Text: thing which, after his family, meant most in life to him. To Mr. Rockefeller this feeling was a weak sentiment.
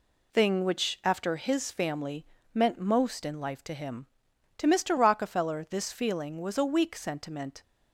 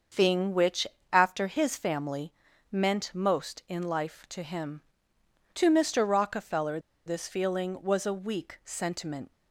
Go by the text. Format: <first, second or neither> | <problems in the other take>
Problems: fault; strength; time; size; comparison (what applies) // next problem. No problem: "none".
first | starts louder than the rest; until 1.3 s; 6.5 dB // pauses between "Rockefeller" and "this"; slight; at 6.7 s; 0.27 s long